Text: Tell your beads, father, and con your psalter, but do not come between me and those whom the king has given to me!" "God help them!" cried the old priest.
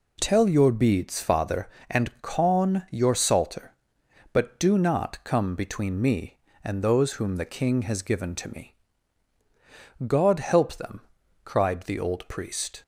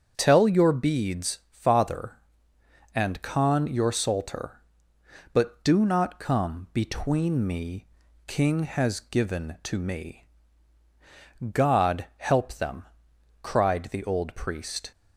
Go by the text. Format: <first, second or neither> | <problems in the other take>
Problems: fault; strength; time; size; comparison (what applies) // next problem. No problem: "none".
first | starts louder than the rest; strong; until 1.1 s; 7.5 dB // skips "and those whom the"; at 8.0 s